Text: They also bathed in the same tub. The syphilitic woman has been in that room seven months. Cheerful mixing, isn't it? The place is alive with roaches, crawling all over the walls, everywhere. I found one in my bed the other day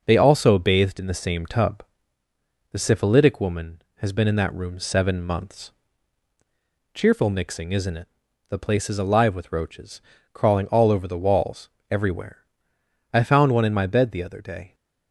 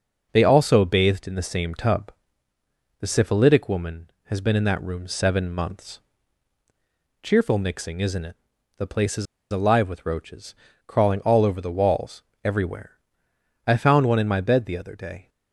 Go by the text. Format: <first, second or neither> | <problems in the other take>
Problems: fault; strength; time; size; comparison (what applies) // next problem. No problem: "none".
first | pauses between "is" and "alive"; slight; at 9.2 s; 0.27 s long